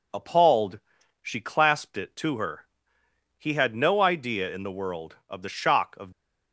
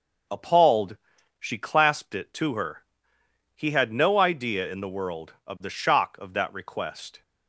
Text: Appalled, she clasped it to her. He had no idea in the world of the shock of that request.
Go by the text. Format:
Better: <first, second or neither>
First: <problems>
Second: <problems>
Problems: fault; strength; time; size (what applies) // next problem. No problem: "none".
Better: second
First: stops before "that request"; at 6.1 s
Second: none